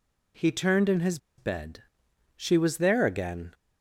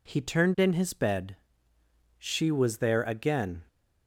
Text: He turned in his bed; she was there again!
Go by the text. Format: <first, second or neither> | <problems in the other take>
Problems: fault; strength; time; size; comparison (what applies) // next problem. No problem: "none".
second | pauses between "his" and "bed"; slight; at 1.1 s; 0.20 s long